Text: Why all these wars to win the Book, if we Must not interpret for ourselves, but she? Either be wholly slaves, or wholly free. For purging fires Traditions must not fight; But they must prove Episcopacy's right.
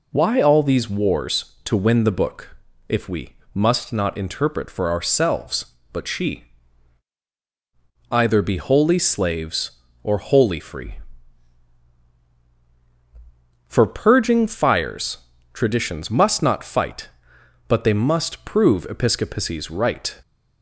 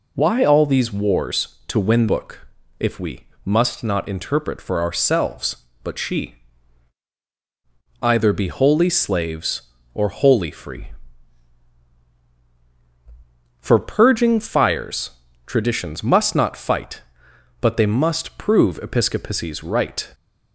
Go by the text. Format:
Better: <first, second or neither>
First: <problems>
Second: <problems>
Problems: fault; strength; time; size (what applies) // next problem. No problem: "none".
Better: first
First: pauses between "we" and "Must"; slight; at 3.3 s; 0.20 s long // pauses between "fires" and "Traditions"; slight; at 15.1 s; 0.36 s long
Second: skips "the"; at 2.0 s // pauses between "we" and "Must"; slight; at 3.2 s; 0.20 s long // pauses between "fires" and "Traditions"; slight; at 15.1 s; 0.36 s long